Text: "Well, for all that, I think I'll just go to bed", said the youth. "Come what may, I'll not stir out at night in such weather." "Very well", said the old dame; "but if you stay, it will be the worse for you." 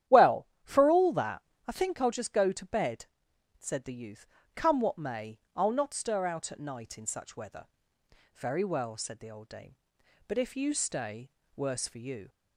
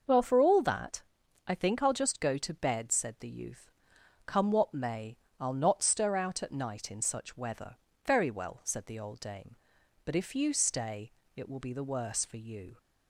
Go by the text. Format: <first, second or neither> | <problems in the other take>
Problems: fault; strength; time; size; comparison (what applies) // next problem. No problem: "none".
second | starts louder than the rest; strong; until 1.2 s; 11 dB; noticeable in the second // skips "it will be the"; at 11.4 s